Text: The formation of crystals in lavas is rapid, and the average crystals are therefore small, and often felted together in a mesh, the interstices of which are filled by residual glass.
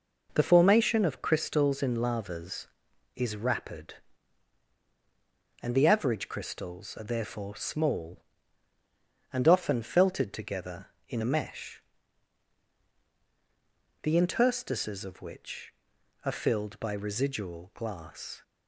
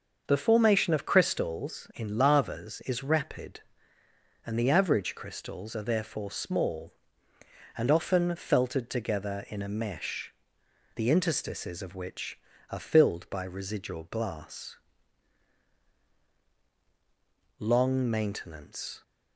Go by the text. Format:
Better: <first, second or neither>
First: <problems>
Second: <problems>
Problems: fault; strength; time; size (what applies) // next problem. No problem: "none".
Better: first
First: none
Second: starts louder than the rest; until 1.2 s; 6.5 dB // goes on to say "Long maintenance"; from 17.5 s on; 1.4 s long